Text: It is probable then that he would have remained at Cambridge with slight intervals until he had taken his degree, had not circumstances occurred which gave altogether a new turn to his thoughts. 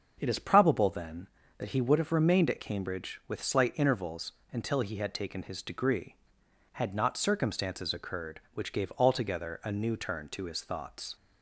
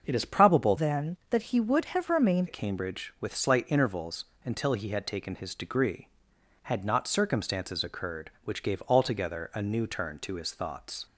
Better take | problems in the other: first | starts louder than the rest; until 1.0 s; 6.5 dB; also in the first // changes voice from "then" to "remained"; from 0.7 to 2.4 s; 1.7 s long // pauses between "intervals" and "until"; slight; at 4.2 s; 0.18 s long; slight in the first

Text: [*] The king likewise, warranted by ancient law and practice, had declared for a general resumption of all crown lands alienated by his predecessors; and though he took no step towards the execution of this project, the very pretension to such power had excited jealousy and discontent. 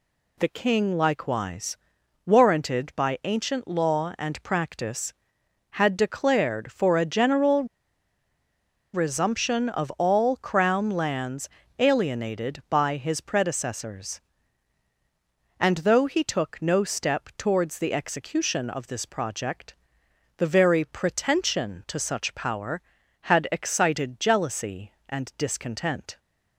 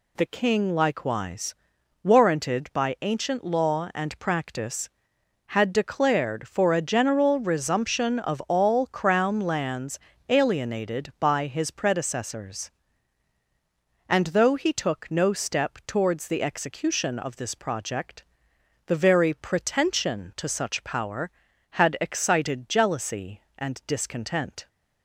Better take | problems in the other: second | pauses between "general" and "resumption"; strong; at 7.6 s; 1.2 s long // pauses between "lands" and "alienated"; slight; at 11.4 s; 0.30 s long; slight in the second

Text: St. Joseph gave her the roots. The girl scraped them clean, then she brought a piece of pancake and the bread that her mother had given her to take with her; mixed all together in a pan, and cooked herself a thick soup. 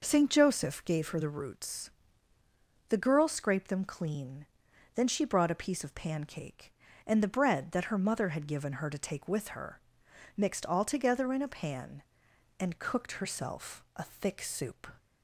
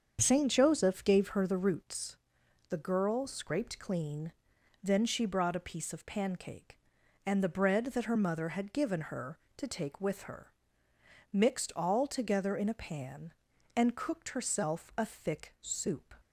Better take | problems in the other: first | starts louder than the rest; strong; until 1.2 s; 7 dB // skips "them"; at 3.7 s

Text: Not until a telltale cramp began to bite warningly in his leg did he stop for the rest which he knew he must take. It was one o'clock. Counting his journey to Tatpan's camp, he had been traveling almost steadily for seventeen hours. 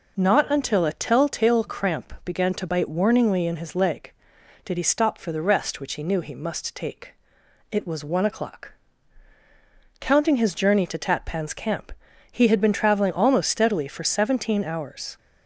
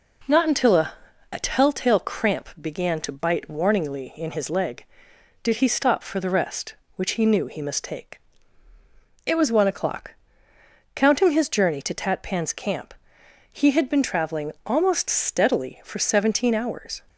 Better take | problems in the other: first | says "a" twice; at 1.3 s

